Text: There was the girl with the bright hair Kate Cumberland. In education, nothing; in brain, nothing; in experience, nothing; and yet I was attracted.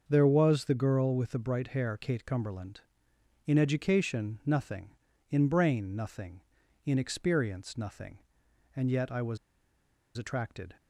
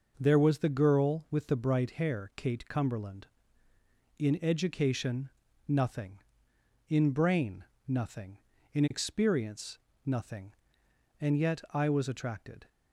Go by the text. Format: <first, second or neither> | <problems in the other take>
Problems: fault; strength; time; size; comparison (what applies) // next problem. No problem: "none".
second | starts louder than the rest; until 1.0 s; 6.5 dB // pauses between "was" and "attracted"; noticeable; at 9.3 s; 0.79 s long